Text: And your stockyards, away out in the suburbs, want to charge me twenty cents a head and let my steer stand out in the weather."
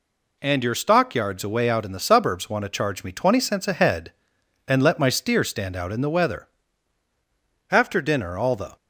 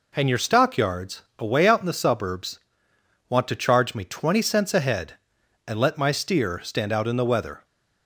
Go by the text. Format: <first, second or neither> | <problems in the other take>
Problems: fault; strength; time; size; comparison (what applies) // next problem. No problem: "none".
second | goes on to say "After dinner all the"; noticeable; from 7.7 s on; 1.0 s long